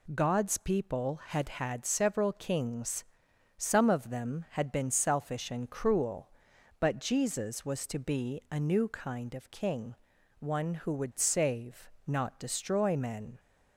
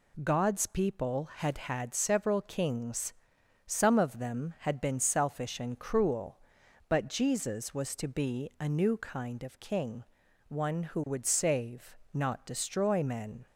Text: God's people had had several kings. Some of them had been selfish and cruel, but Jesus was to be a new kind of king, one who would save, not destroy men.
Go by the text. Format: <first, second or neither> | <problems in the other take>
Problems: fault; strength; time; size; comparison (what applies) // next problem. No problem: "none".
neither | none